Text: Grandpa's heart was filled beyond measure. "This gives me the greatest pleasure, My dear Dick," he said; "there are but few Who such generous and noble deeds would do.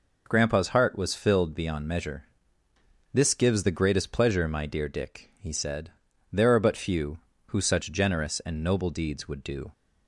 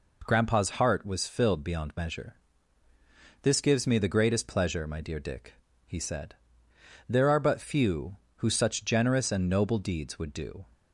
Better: second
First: skips "me"; at 3.6 s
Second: none

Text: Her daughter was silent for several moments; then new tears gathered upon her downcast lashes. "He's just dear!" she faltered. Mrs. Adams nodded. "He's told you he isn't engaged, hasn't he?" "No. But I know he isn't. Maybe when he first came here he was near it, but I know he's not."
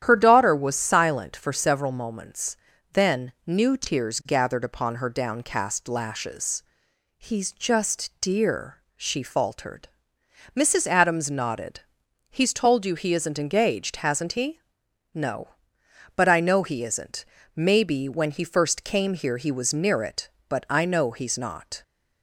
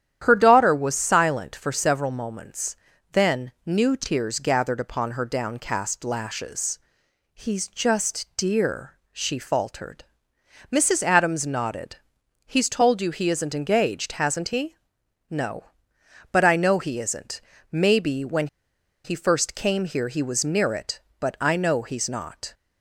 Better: first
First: starts louder than the rest; strong; until 1.0 s; 10.5 dB // pauses between "then" and "new"; slight; at 3.3 s; 0.16 s long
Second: starts louder than the rest; strong; until 1.2 s; 10.5 dB // pauses between "then" and "new"; slight; at 3.5 s; 0.16 s long // pauses between "when" and "he"; noticeable; at 18.4 s; 0.58 s long

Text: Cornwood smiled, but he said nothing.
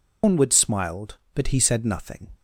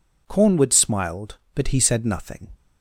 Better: second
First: loses the start of "Cornwood"; at 0.2 s; 170 ms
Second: none

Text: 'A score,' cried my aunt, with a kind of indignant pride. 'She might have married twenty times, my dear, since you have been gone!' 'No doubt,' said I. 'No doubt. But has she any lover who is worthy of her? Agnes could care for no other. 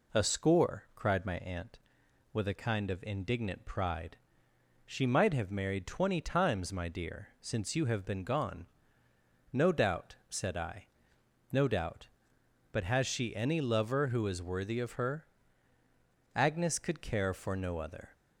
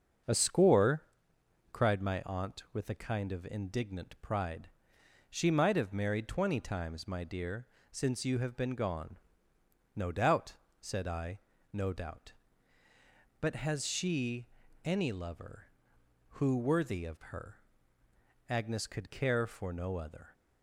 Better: first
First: none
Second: starts louder than the rest; until 1.9 s; 6.5 dB // pauses between "she" and "any"; at 14.4 s; 0.38 s long // skips "is"; at 16.5 s

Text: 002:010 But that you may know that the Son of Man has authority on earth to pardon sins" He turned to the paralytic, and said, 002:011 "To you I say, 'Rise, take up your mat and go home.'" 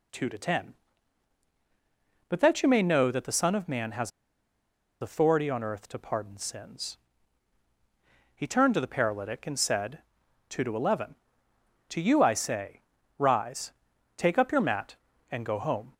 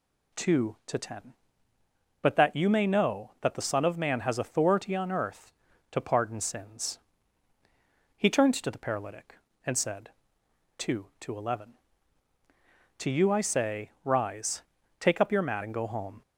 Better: second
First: pauses between "has" and "authority"; noticeable; at 4.1 s; 0.91 s long // pauses between "sins" and "He"; strong; at 6.9 s; 1.3 s long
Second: pauses between "sins" and "He"; at 6.9 s; 1.1 s long

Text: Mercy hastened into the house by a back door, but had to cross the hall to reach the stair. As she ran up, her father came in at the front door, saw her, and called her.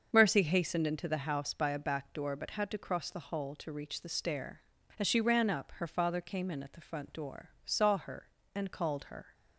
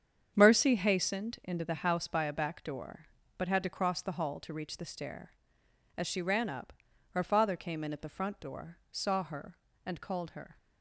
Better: neither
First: starts louder than the rest; until 1.1 s; 6.5 dB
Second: starts louder than the rest; strong; until 1.3 s; 8 dB

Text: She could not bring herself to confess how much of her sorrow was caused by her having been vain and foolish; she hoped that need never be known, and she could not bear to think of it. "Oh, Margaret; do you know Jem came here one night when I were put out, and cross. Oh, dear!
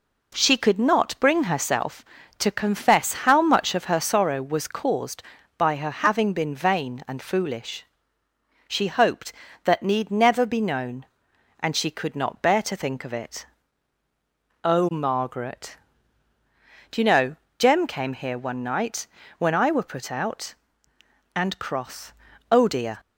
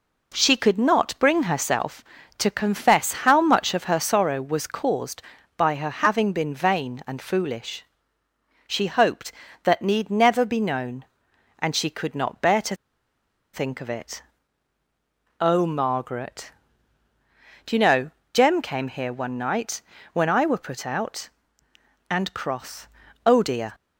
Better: first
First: pauses between "know" and "Jem"; slight; at 17.3 s; 0.20 s long // pauses between "night" and "when"; slight; at 19.0 s; 0.32 s long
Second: pauses between "to" and "think"; noticeable; at 12.7 s; 0.78 s long // pauses between "know" and "Jem"; slight; at 18.1 s; 0.20 s long // pauses between "night" and "when"; slight; at 19.8 s; 0.32 s long

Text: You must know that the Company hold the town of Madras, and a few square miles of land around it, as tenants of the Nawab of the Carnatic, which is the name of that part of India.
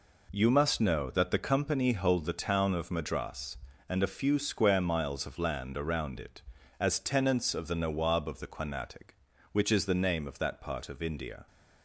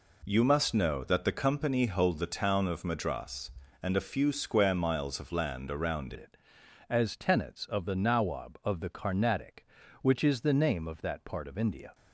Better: first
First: none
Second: changes voice at "it"; from 6.1 s on; 5.8 s long

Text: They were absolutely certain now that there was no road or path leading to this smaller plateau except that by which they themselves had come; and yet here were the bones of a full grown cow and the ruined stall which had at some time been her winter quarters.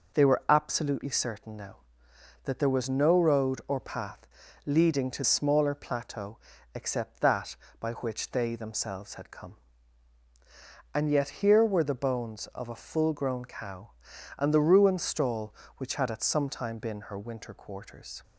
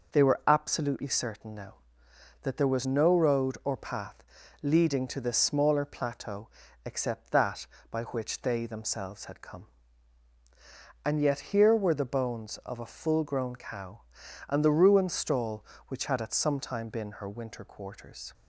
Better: second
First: pauses between "path" and "leading"; at 4.2 s; 0.38 s long // skips "this"; at 5.2 s // pauses between "plateau" and "except"; slight; at 6.3 s; 0.36 s long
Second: pauses between "path" and "leading"; at 4.2 s; 0.38 s long // pauses between "plateau" and "except"; slight; at 6.4 s; 0.36 s long

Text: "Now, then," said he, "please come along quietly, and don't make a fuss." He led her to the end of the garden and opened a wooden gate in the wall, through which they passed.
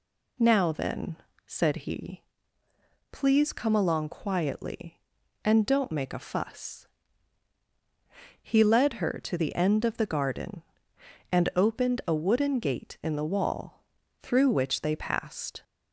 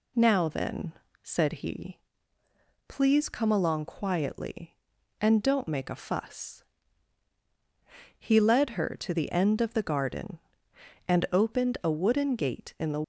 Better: first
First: none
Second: stops before "wall through which they passed"; at 13.0 s

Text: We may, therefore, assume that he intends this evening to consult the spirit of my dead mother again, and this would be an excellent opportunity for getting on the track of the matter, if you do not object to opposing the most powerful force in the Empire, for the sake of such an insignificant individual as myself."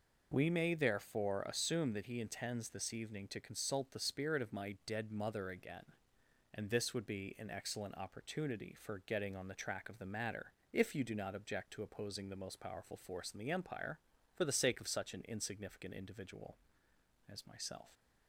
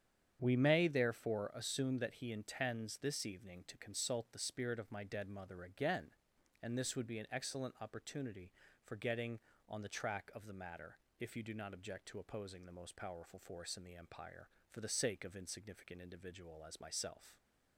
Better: first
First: none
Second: starts louder than the rest; strong; until 1.4 s; 8.5 dB // skips "such an"; at 15.3 s

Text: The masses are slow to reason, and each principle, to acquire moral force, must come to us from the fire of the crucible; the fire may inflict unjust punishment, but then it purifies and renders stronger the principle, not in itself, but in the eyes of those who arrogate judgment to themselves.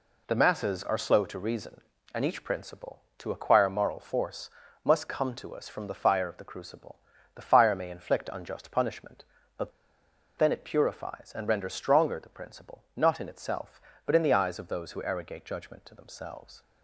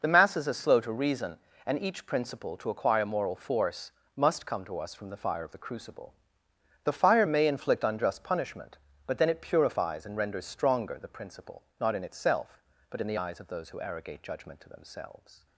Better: second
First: pauses between "but" and "then"; noticeable; at 9.7 s; 0.66 s long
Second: none

